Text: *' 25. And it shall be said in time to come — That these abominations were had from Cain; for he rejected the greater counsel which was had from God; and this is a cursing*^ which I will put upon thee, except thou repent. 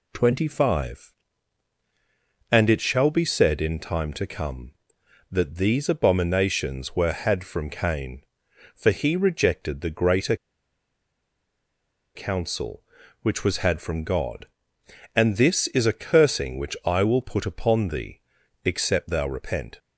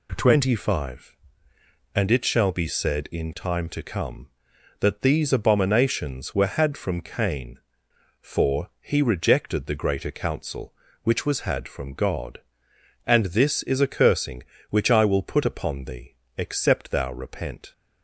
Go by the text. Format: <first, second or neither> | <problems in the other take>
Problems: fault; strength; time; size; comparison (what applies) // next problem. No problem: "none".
second | pauses between "greater" and "counsel"; strong; at 10.3 s; 1.8 s long